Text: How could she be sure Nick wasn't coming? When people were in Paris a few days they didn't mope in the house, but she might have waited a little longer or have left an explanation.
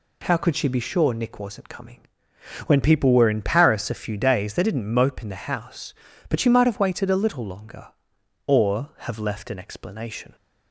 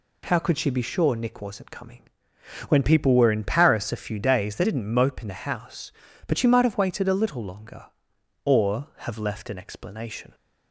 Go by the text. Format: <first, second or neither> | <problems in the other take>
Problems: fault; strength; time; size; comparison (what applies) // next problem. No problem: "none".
neither | none